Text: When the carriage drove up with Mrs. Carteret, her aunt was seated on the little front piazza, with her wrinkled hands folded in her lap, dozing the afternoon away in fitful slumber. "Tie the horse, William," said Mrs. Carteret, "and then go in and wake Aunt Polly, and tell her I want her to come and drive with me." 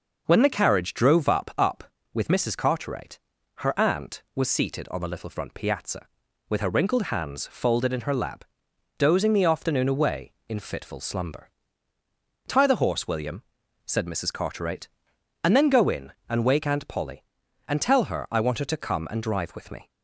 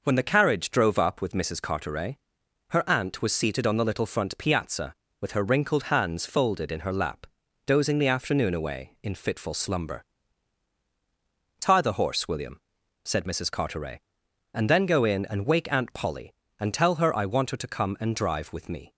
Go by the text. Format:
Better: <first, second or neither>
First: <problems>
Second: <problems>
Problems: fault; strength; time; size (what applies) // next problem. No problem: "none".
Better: second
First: says "up" twice; at 1.5 s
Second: none